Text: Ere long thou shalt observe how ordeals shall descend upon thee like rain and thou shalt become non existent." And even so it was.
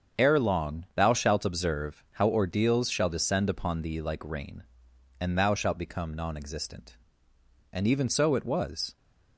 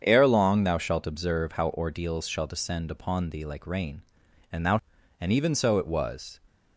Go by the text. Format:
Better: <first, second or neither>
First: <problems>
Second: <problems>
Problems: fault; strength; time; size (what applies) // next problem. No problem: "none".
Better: first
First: starts louder than the rest; strong; until 1.2 s; 7.5 dB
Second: starts louder than the rest; strong; until 1.0 s; 7.5 dB // skips "shalt become non existent"; at 4.9 s